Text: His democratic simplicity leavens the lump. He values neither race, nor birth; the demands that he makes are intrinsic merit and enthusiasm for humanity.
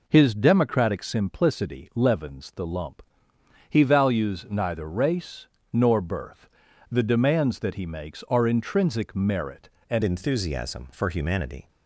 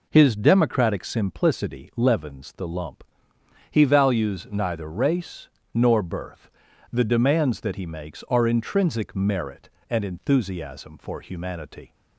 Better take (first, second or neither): second